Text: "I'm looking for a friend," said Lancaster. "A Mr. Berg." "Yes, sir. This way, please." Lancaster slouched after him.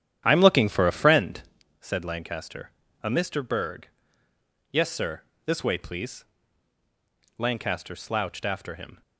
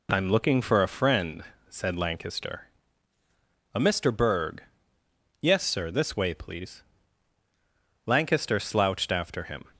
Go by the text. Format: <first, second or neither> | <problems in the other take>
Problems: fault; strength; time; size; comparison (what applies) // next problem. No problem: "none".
second | starts louder than the rest; strong; until 1.6 s; 10 dB